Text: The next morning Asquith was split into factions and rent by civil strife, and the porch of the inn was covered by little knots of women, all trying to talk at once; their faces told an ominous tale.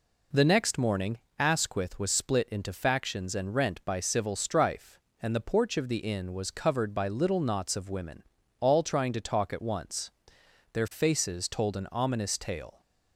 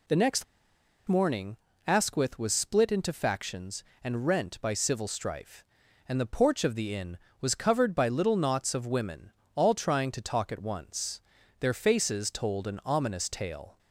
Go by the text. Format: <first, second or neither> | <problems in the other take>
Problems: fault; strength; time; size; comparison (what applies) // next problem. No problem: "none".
first | pauses between "next" and "morning"; noticeable; at 0.4 s; 0.63 s long // pauses between "morning" and "Asquith"; slight; at 1.5 s; 0.28 s long; slight in the first